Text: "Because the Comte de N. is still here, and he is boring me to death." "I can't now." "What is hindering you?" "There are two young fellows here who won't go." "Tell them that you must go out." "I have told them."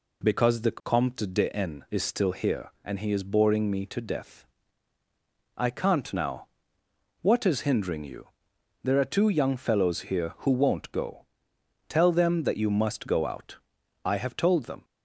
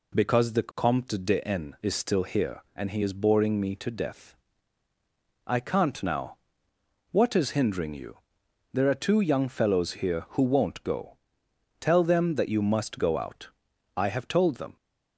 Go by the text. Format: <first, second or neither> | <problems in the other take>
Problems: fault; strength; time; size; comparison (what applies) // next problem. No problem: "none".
neither | none